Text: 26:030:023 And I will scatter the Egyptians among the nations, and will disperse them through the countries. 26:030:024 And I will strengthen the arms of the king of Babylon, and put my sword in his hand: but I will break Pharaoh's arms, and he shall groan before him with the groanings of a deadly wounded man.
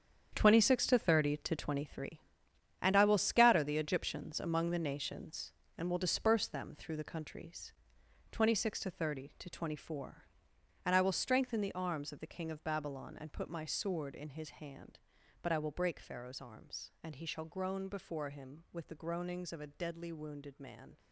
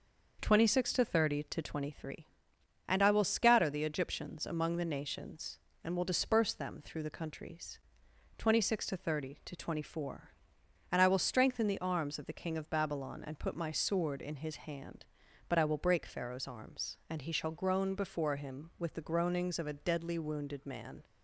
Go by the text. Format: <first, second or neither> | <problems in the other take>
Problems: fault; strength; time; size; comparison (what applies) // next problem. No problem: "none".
second | gets quieter; strong; throughout; 12 dB